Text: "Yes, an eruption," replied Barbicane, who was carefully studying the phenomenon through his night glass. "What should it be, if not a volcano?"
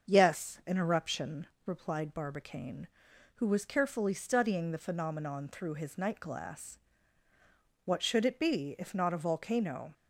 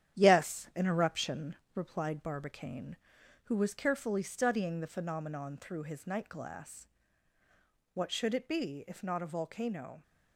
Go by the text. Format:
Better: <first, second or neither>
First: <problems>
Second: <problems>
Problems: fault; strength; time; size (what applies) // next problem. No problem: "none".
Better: first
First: starts louder than the rest; until 1.1 s; 7 dB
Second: gets quieter; noticeable; throughout; 5.5 dB // starts louder than the rest; strong; until 1.2 s; 10.5 dB